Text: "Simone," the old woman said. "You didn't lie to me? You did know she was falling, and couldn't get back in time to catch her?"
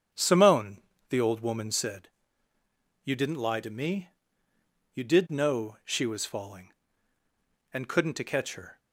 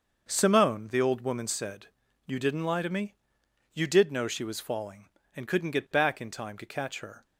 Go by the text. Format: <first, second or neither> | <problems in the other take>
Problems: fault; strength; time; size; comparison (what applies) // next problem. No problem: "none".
second | starts louder than the rest; strong; until 1.4 s; 7.5 dB; also in the second // skips "get back in time"; at 8.1 s